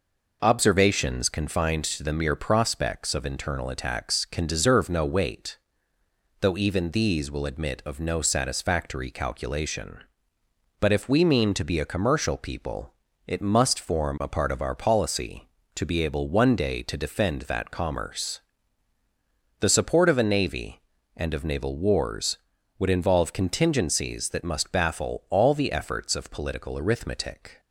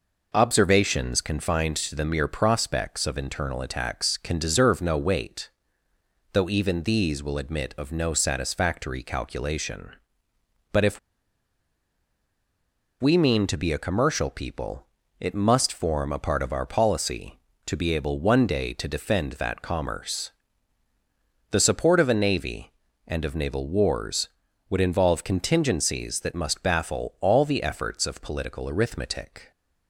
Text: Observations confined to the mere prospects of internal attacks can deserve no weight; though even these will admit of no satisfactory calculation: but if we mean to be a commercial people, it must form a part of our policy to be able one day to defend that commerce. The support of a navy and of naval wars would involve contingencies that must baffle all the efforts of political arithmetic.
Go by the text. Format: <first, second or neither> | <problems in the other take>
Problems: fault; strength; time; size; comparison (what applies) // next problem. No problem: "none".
first | pauses between "if" and "we"; strong; at 10.9 s; 2.0 s long